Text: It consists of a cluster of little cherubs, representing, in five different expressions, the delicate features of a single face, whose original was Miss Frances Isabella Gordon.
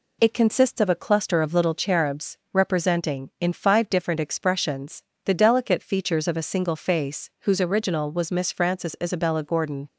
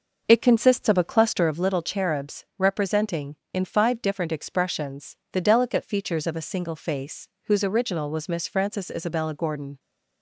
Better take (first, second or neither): first